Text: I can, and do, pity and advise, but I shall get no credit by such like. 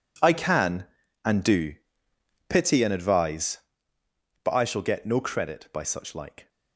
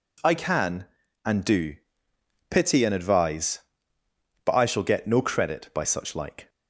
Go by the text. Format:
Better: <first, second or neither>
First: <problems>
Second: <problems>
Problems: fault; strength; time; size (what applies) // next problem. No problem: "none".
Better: second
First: gets quieter; strong; throughout; 15 dB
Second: none